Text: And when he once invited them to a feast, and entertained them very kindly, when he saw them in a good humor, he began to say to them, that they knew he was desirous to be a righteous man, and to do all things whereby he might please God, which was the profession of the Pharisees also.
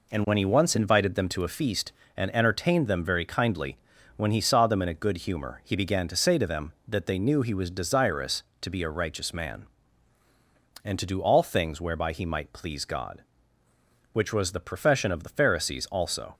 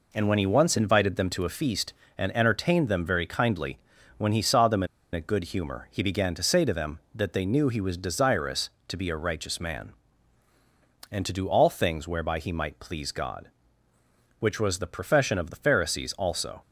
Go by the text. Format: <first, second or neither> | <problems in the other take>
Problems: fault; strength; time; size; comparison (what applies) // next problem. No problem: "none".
first | pauses between "in" and "a"; slight; at 4.8 s; 0.28 s long